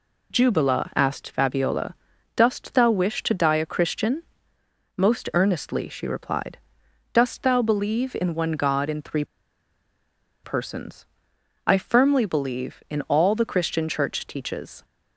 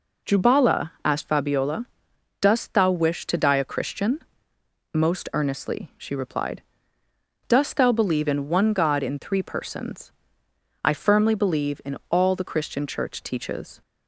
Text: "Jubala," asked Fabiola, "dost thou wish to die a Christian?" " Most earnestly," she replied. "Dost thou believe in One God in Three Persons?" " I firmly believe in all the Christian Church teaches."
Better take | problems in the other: second | pauses between "Three" and "Persons"; at 9.2 s; 1.1 s long

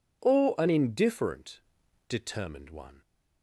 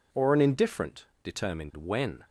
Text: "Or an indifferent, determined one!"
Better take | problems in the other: first | says "when" for "one"; at 1.7 s

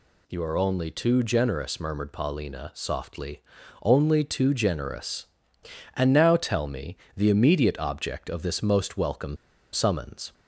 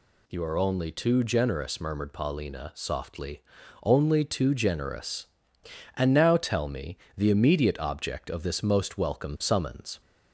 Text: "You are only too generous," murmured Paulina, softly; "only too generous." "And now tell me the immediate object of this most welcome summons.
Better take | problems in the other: second | pauses between "me" and "the"; slight; at 6.9 s; 0.18 s long; slight in the second // pauses between "welcome" and "summons"; at 9.3 s; 0.36 s long

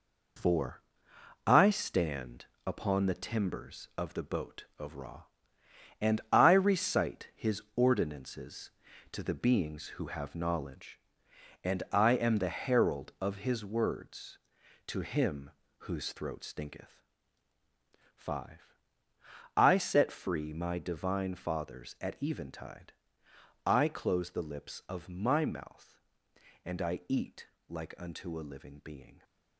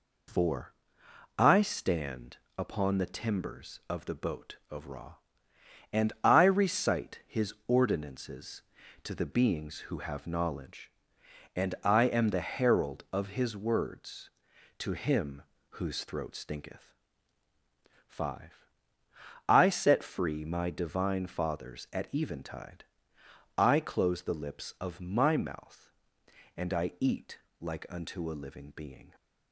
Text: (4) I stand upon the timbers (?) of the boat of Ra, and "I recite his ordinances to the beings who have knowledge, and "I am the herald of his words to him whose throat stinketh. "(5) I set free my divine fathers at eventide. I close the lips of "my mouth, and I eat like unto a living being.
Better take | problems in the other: second | gets quieter; throughout; 6.5 dB // pauses between "stand" and "upon"; slight; at 2.4 s; 0.18 s long; slight in the second // pauses between "him" and "whose"; slight; at 15.4 s; 0.30 s long; slight in the second // pauses between "eat" and "like"; slight; at 27.4 s; 0.20 s long; slight in the second

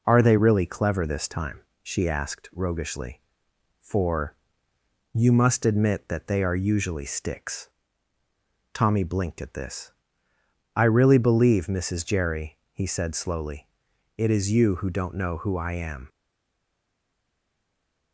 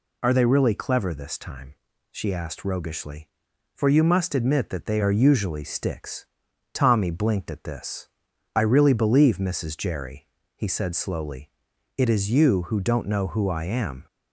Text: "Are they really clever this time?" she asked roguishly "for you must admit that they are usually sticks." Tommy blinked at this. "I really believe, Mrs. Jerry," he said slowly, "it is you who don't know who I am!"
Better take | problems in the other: second | pauses between "for" and "you"; noticeable; at 4.3 s; 0.78 s long // stays silent after the last word; noticeable; from 16.0 s on; 2.1 s long

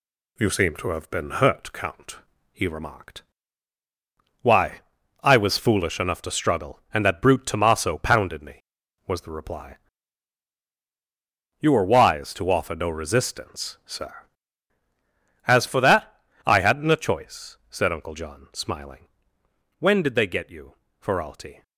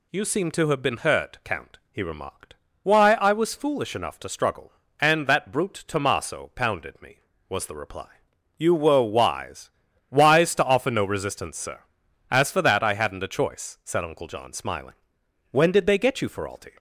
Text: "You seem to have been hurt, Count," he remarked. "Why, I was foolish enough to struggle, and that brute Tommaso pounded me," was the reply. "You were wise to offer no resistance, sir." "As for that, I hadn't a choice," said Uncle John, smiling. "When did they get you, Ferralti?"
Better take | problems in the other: first | says "wise" twice; at 10.0 s

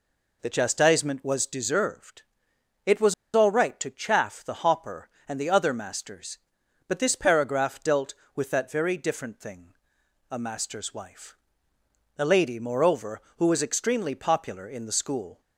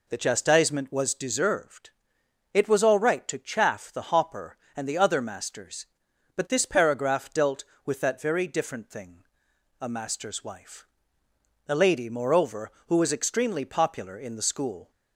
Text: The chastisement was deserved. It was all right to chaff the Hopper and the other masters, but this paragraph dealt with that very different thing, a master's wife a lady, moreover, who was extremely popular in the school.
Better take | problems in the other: second | pauses between "was" and "all"; slight; at 3.1 s; 0.20 s long // pauses between "wife" and "a"; noticeable; at 11.3 s; 0.82 s long; noticeable in the second

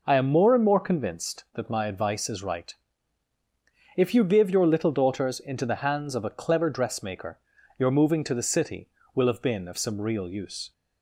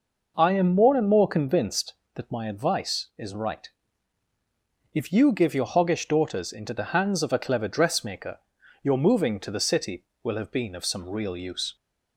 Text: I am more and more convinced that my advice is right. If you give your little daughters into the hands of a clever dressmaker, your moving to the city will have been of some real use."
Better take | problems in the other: first | says "hoggish" for "little"; at 5.6 s

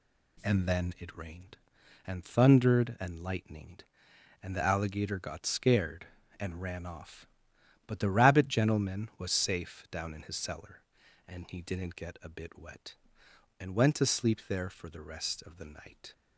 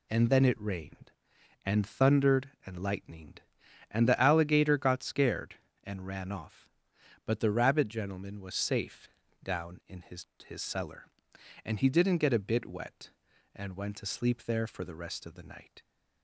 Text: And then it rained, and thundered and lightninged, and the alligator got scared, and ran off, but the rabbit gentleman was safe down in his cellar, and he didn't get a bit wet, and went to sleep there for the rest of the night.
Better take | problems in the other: first | pauses between "safe" and "down"; slight; at 9.0 s; 0.34 s long // says "his" twice; at 10.4 s

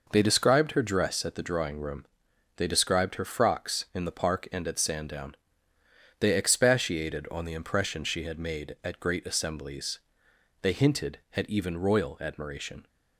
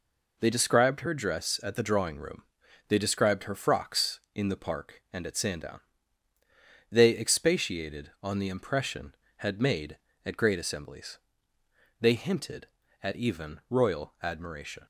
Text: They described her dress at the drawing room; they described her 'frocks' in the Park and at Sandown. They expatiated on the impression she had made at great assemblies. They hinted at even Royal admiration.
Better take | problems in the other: first | skips "she"; at 9.2 s

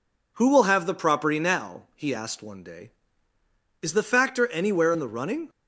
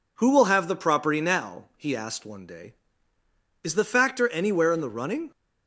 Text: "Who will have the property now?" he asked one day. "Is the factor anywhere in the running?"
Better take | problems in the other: neither | none

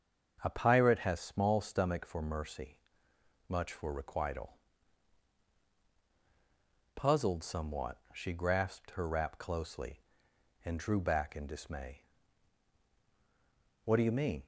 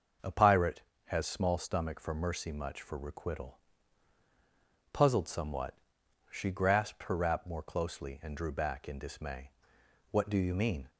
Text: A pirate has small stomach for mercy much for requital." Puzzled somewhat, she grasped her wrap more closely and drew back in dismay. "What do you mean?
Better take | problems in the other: second | starts louder than the rest; until 1.4 s; 6.5 dB; also in the second // pauses between "mercy" and "much"; noticeable; at 2.7 s; 0.72 s long // skips "more"; at 9.3 s

